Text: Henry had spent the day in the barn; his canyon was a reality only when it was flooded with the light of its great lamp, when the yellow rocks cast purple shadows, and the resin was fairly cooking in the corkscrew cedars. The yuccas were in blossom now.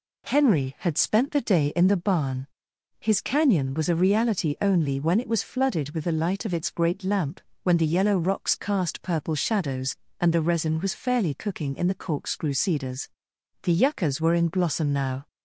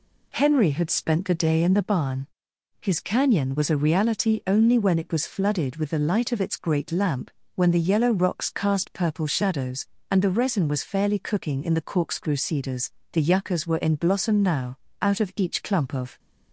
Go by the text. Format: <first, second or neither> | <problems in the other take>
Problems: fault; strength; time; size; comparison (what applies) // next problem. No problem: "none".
first | goes on to say "Out of each clump of"; noticeable; from 15.0 s on; 1.1 s long